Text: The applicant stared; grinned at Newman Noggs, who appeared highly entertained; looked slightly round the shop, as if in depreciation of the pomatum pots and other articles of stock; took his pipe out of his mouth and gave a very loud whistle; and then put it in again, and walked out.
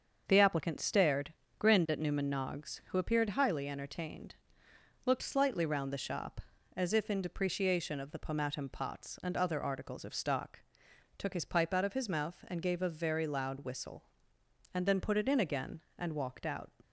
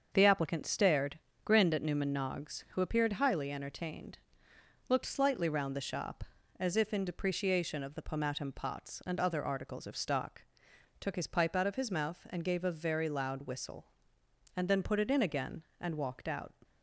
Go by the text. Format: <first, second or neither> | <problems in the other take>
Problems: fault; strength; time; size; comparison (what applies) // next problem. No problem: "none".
neither | starts louder than the rest; the same in both